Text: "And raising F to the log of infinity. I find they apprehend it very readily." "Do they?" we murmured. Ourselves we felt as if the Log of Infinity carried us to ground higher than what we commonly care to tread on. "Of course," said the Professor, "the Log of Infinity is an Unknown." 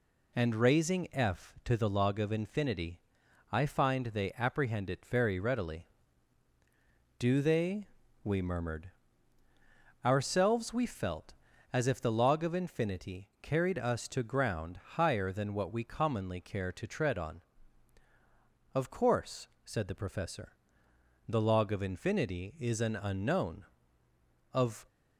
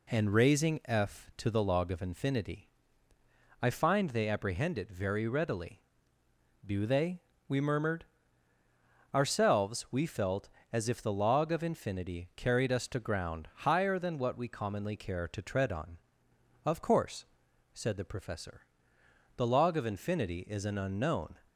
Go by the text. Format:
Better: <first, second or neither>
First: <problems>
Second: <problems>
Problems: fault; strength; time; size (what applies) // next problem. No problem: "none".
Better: second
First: pauses between "ground" and "higher"; slight; at 14.7 s; 0.18 s long // goes on to say "Of"; slight; from 24.5 s on; 0.32 s long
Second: none